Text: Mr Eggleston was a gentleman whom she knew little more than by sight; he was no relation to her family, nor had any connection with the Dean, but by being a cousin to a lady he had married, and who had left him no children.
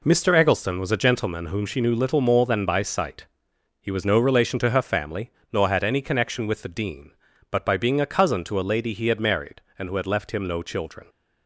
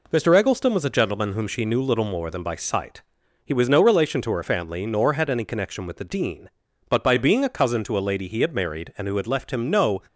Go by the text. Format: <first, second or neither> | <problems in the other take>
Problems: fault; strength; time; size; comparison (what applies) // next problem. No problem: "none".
first | stops before "children"; at 10.0 s